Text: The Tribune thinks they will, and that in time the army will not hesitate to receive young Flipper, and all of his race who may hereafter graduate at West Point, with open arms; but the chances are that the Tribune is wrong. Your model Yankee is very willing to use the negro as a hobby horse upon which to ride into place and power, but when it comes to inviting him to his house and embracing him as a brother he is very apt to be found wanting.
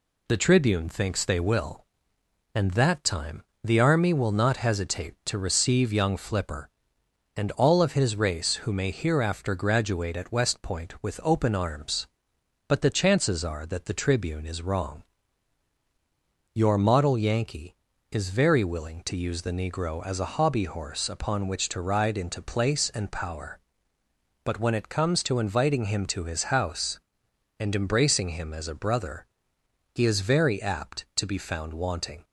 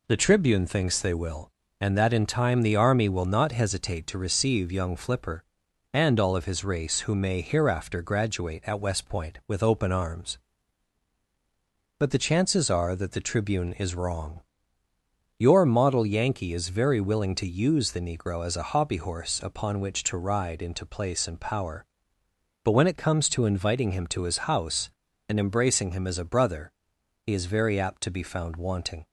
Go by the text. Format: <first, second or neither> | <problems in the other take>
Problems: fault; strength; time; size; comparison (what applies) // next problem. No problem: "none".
second | skips "in"; at 3.0 s // pauses between "time" and "the"; slight; at 3.4 s; 0.20 s long // pauses between "brother" and "he"; noticeable; at 29.2 s; 0.70 s long; noticeable in the second